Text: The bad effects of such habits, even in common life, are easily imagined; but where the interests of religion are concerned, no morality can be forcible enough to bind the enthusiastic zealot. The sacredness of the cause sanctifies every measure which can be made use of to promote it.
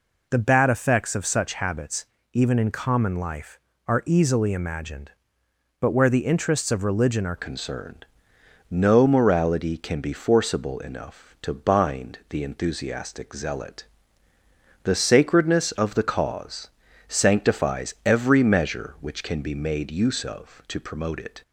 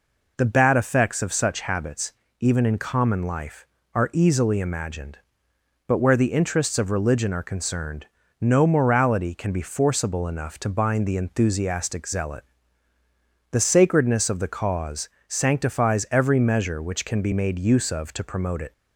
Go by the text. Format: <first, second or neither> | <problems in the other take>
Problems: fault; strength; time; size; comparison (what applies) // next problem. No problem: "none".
second | changes voice at "concerned"; from 7.3 s on; 14.1 s long // pauses between "cause" and "sanctifies"; at 16.6 s; 0.40 s long; slight in the second